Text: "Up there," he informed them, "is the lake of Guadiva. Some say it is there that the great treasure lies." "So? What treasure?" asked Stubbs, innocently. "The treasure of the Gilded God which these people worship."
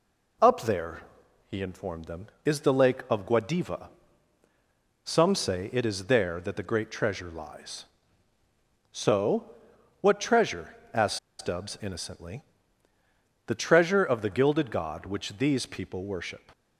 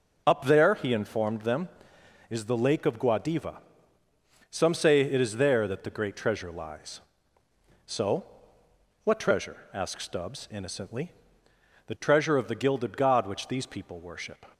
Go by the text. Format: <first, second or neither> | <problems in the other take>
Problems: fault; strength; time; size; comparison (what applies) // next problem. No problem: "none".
second | pauses between "asked" and "Stubbs"; slight; at 11.1 s; 0.22 s long